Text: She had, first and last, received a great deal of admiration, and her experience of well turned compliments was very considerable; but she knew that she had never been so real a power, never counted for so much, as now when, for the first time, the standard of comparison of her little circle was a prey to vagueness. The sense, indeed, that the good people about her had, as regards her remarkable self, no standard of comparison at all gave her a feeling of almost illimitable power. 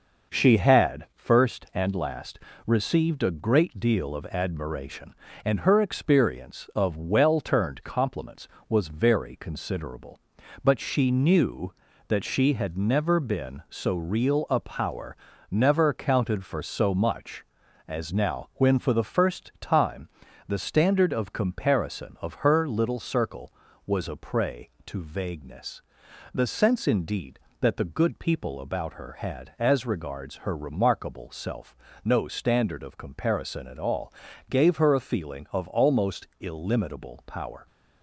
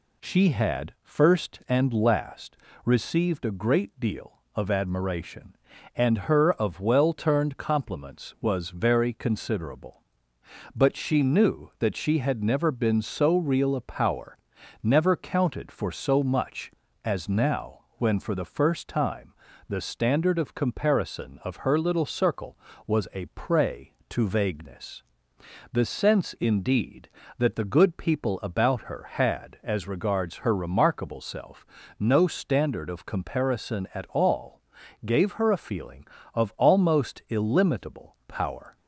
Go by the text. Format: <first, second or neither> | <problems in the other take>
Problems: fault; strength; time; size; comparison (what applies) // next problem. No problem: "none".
first | skips "experience"; at 6.5 s // pauses between "now" and "when"; slight; at 17.7 s; 0.18 s long // pauses between "all" and "gave"; at 34.6 s; 0.44 s long; slight in the first